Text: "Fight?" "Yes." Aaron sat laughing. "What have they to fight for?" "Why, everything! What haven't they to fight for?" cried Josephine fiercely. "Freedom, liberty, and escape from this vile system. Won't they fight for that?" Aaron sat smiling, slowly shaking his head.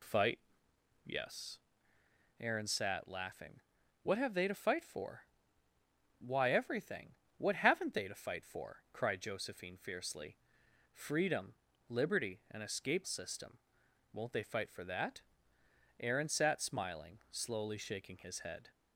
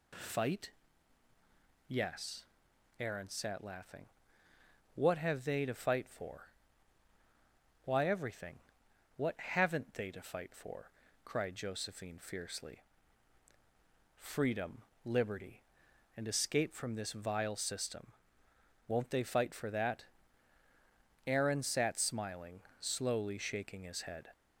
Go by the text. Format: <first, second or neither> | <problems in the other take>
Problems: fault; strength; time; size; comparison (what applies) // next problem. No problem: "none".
second | skips "from this vile"; at 13.0 s